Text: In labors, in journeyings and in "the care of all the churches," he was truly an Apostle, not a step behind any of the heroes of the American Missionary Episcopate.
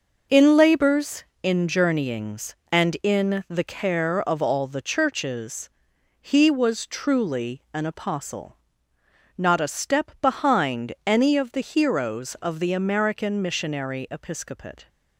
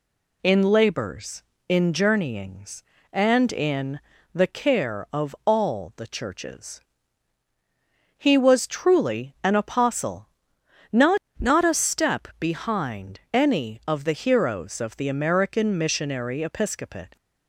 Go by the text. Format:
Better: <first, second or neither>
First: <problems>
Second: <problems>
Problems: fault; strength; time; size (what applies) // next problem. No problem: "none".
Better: first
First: none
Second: pauses between "in" and "the"; slight; at 3.9 s; 0.34 s long // says "not" twice; at 11.3 s